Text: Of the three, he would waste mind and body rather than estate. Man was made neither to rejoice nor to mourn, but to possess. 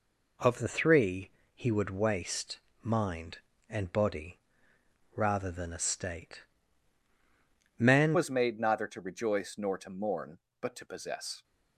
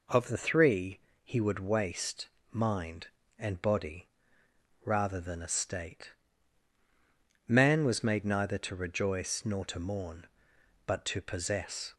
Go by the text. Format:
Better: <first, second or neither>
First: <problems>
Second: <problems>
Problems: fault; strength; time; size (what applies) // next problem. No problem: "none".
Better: second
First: pauses between "waste" and "mind"; slight; at 2.5 s; 0.24 s long // pauses between "body" and "rather"; noticeable; at 4.3 s; 0.76 s long // changes voice at "was"; from 8.1 s on; 3.3 s long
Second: pauses between "waste" and "mind"; slight; at 2.2 s; 0.24 s long // pauses between "body" and "rather"; noticeable; at 4.0 s; 0.76 s long